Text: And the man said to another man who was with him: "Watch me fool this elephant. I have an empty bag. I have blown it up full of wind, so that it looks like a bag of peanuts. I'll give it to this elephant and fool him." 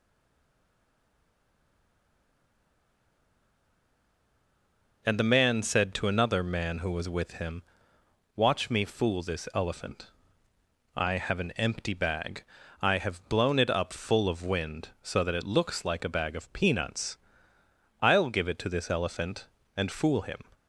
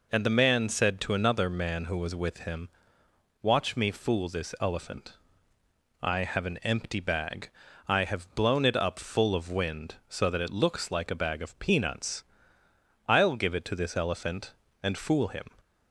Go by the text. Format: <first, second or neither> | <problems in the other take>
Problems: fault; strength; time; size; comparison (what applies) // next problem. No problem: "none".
second | stays silent before the first word; strong; until 5.0 s; 5.0 s long